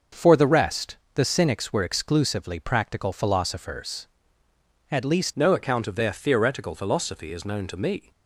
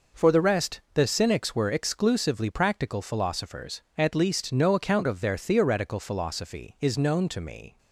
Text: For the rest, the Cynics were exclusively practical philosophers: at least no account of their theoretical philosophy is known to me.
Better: second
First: starts louder than the rest; noticeable; until 1.3 s; 6 dB // changes voice at "no"; from 5.3 s on; 2.8 s long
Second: none

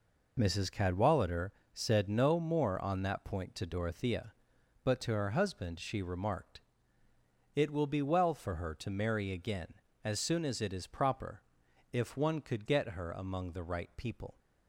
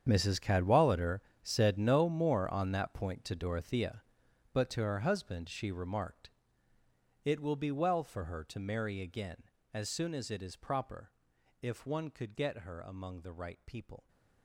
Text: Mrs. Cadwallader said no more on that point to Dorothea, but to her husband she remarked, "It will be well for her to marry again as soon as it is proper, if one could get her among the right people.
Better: first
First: pauses between "Cadwallader" and "said"; slight; at 1.5 s; 0.24 s long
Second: gets quieter; strong; throughout; 16.5 dB // pauses between "Cadwallader" and "said"; slight; at 1.1 s; 0.24 s long

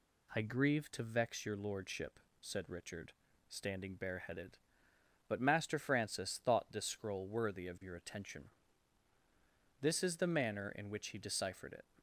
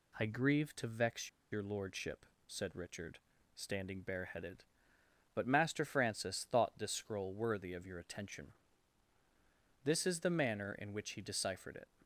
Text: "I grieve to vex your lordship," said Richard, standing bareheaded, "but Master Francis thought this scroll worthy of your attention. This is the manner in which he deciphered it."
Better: first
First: none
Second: pauses between "vex" and "your"; slight; at 1.2 s; 0.24 s long

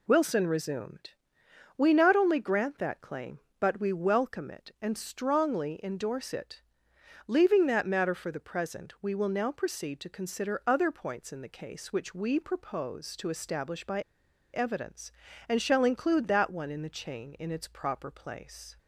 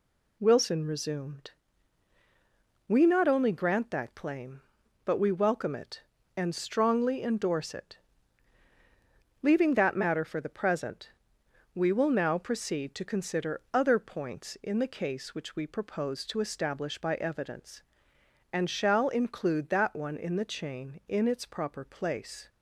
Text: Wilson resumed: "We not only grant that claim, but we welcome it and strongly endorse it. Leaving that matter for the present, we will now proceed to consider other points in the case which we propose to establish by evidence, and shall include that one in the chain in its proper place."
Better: second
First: pauses between "by" and "evidence"; noticeable; at 14.0 s; 0.52 s long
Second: none

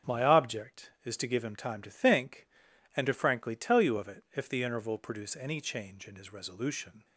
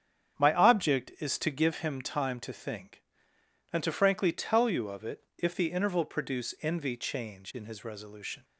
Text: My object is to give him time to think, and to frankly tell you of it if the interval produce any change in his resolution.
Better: first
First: starts louder than the rest; strong; until 1.1 s; 7.5 dB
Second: starts louder than the rest; strong; until 1.4 s; 8.5 dB // says "envy" for "any"; at 6.6 s

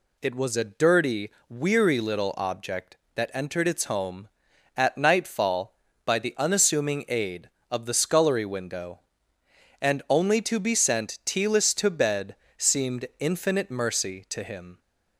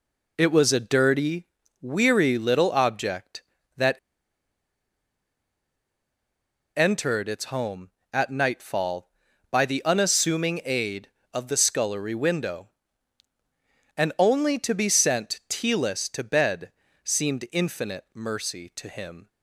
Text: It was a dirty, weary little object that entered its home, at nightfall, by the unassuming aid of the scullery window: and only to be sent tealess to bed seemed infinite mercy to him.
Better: first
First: pauses between "bed" and "seemed"; slight; at 12.3 s; 0.22 s long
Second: pauses between "that" and "entered"; strong; at 3.9 s; 2.8 s long // pauses between "bed" and "seemed"; slight; at 16.7 s; 0.32 s long

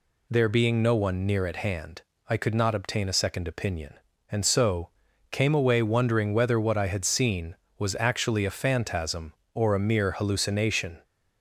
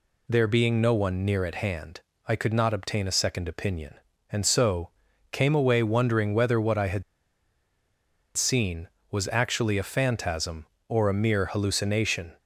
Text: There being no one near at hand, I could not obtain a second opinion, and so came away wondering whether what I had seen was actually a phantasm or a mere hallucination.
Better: first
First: pauses between "so" and "came"; at 4.8 s; 0.42 s long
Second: pauses between "so" and "came"; at 4.8 s; 0.42 s long // pauses between "had" and "seen"; strong; at 7.0 s; 1.3 s long

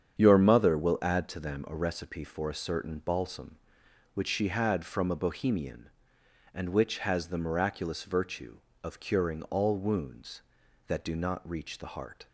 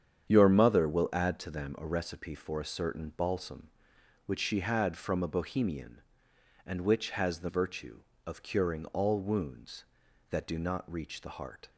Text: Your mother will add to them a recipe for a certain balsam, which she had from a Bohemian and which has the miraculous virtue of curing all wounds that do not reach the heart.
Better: first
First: starts louder than the rest; strong; until 1.2 s; 8 dB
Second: starts louder than the rest; strong; until 1.3 s; 8.5 dB // skips "miraculous"; at 7.4 s

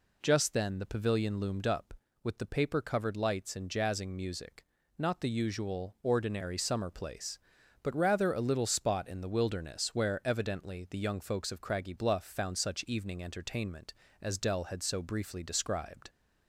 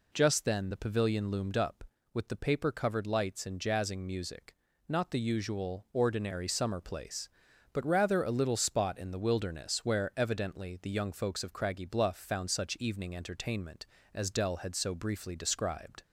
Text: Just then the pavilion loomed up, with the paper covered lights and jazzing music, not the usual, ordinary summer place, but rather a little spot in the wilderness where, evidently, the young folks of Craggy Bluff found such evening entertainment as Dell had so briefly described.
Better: neither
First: none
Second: none

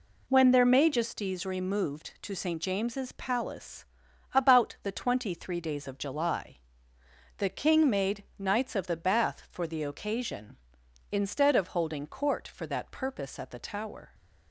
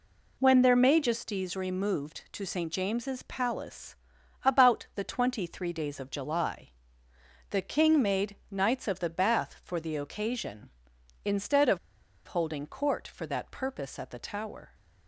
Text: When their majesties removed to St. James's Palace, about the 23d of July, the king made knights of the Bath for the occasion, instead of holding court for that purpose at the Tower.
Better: first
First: pauses between "made" and "knights"; slight; at 8.2 s; 0.16 s long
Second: pauses between "made" and "knights"; slight; at 8.3 s; 0.16 s long // pauses between "of" and "holding"; noticeable; at 11.7 s; 0.49 s long

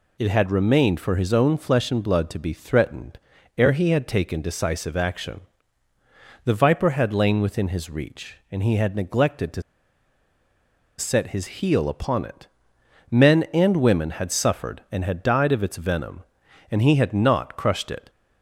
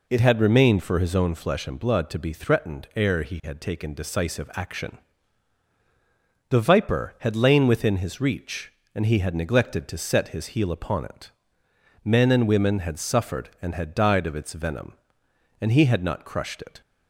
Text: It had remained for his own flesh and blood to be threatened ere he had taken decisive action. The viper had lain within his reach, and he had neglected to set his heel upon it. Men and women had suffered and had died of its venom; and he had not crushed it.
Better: second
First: pauses between "threatened" and "ere"; at 3.1 s; 0.40 s long // pauses between "to" and "set"; strong; at 9.6 s; 1.3 s long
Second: none

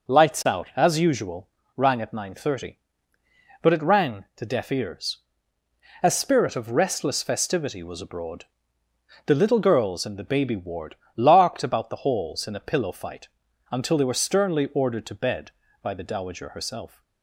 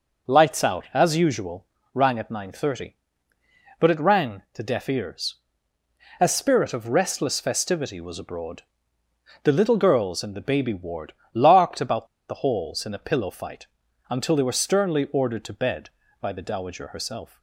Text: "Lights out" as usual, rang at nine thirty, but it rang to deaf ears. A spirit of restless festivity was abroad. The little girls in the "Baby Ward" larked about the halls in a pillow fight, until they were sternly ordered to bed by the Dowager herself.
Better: first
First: pauses between "Ward" and "larked"; slight; at 10.9 s; 0.20 s long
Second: pauses between "Ward" and "larked"; slight; at 11.1 s; 0.20 s long // pauses between "about" and "the"; slight; at 12.0 s; 0.23 s long

